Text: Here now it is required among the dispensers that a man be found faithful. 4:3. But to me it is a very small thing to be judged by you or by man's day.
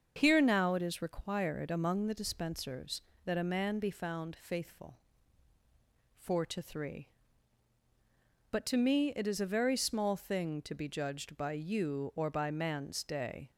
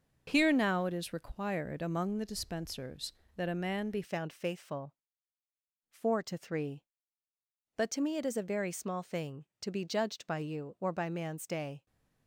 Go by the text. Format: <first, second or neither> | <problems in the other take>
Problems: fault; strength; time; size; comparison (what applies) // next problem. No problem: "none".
first | starts louder than the rest; until 1.2 s; 6 dB; also in the first // changes voice at "found"; from 4.0 s on; 7.8 s long